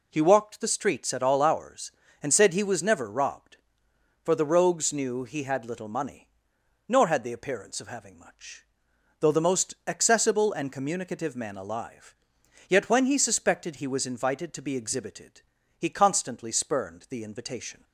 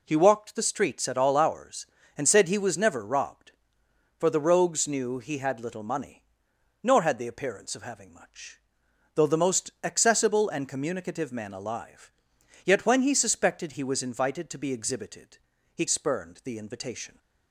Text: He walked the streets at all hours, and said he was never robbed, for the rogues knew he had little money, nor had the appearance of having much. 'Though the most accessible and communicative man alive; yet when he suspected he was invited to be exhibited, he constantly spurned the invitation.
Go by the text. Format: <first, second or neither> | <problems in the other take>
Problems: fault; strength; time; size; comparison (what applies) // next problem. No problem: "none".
first | skips "constantly"; at 15.8 s